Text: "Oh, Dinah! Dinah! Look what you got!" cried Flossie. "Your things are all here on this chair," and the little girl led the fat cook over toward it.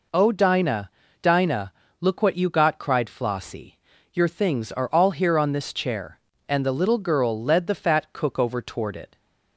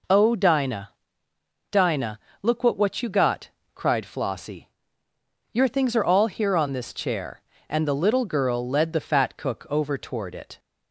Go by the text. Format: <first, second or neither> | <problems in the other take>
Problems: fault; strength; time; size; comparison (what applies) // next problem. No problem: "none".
first | says "what" twice; at 2.7 s